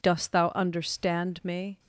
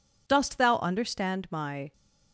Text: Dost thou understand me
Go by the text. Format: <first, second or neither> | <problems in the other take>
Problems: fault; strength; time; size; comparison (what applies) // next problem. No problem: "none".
first | says "my" for "me"; at 1.5 s